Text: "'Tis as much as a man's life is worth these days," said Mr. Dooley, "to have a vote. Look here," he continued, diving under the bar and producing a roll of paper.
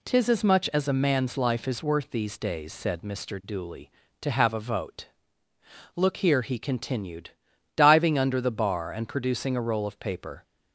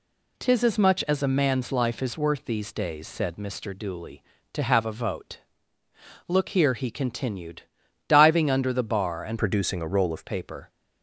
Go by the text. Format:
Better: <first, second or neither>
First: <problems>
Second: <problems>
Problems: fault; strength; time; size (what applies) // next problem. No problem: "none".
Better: first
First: none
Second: changes voice from "producing" to "of"; from 9.3 to 10.2 s; 0.9 s long